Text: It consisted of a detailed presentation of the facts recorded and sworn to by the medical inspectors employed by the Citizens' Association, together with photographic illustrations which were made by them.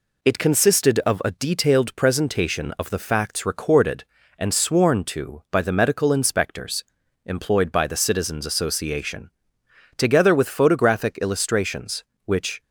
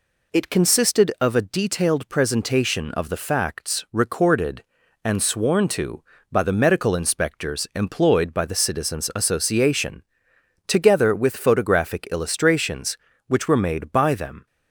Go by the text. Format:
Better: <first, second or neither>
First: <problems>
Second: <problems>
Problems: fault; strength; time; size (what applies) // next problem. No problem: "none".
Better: second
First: pauses between "inspectors" and "employed"; at 6.8 s; 0.42 s long // stops before "were made by them"; at 12.6 s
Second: none